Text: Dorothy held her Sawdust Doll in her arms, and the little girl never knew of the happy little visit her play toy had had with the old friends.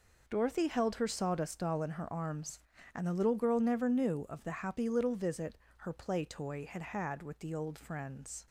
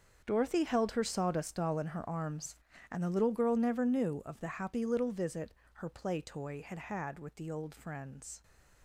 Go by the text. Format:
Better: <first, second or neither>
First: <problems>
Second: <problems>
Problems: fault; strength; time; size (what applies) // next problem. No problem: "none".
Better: first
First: pauses between "visit" and "her"; slight; at 5.5 s; 0.22 s long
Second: gets quieter; strong; throughout; 14.5 dB // pauses between "visit" and "her"; slight; at 5.5 s; 0.22 s long